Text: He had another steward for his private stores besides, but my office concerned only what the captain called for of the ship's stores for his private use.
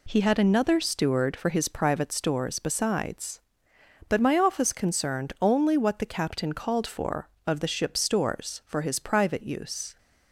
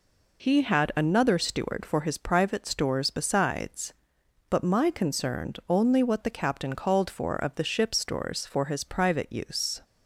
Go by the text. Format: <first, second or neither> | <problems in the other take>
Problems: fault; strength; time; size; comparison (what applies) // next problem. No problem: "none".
first | skips "office"; at 4.8 s